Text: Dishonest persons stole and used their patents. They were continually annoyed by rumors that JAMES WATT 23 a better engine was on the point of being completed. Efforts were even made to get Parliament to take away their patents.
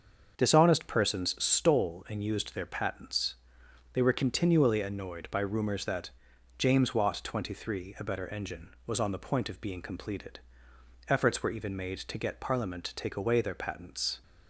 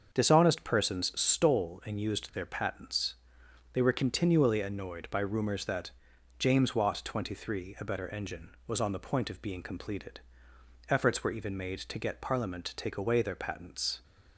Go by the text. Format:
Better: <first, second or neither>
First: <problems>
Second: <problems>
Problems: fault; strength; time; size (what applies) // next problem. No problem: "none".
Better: neither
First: starts louder than the rest; until 1.4 s; 6.5 dB // pauses between "that" and "JAMES"; noticeable; at 6.0 s; 0.48 s long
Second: starts louder than the rest; until 1.2 s; 7 dB // pauses between "that" and "JAMES"; noticeable; at 5.8 s; 0.48 s long